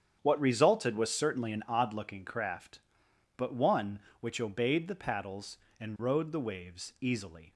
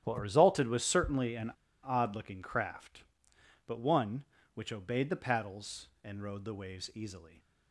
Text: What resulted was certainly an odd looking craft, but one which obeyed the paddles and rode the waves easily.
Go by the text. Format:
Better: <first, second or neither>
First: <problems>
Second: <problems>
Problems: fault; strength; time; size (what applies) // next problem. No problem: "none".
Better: first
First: starts louder than the rest; strong; until 1.2 s; 8.5 dB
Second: starts louder than the rest; strong; until 1.0 s; 11 dB // pauses between "an" and "odd"; slight; at 1.5 s; 0.33 s long